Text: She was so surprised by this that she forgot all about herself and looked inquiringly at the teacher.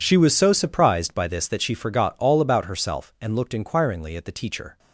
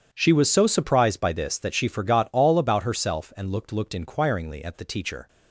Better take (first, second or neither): first